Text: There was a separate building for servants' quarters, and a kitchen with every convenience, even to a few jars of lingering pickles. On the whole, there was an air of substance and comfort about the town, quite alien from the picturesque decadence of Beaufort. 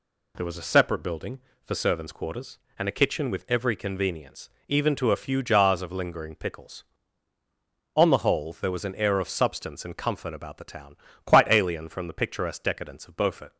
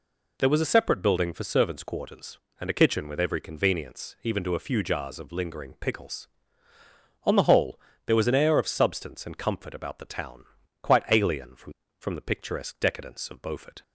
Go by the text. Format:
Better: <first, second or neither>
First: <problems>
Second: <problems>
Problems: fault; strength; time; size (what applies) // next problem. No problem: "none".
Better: first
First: none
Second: says "from" twice; at 12.0 s